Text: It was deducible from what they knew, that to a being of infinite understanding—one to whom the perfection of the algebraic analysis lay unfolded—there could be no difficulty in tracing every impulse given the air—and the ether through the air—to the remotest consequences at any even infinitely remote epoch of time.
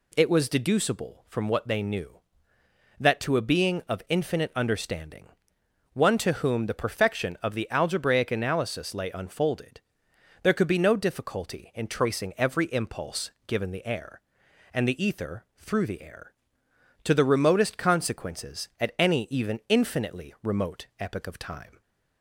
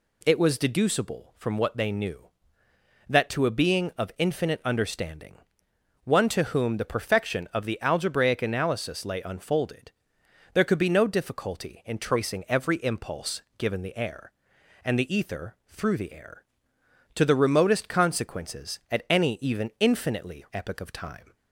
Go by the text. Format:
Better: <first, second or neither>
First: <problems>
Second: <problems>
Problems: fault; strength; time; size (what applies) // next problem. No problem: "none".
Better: first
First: pauses between "impulse" and "given"; slight; at 13.3 s; 0.16 s long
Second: pauses between "impulse" and "given"; slight; at 13.4 s; 0.16 s long // skips "remote"; at 20.4 s